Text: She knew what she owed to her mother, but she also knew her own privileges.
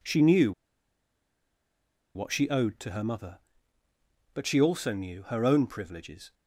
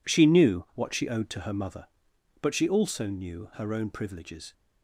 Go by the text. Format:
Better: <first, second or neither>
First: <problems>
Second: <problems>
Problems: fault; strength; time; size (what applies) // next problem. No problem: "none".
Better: second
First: pauses between "knew" and "what"; strong; at 0.5 s; 1.6 s long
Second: none